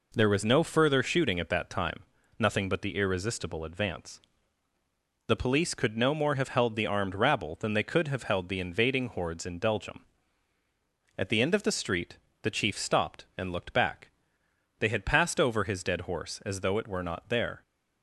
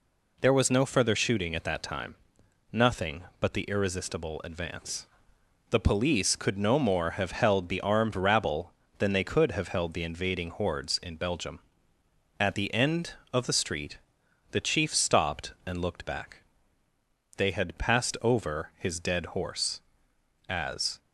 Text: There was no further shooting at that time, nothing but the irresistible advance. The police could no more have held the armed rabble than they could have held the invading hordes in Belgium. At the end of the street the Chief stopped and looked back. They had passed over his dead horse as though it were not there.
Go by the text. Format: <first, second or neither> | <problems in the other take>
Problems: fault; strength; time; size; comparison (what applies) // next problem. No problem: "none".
first | pauses between "street" and "the"; noticeable; at 13.9 s; 0.52 s long; slight in the first // stops before "though it were not there"; at 20.9 s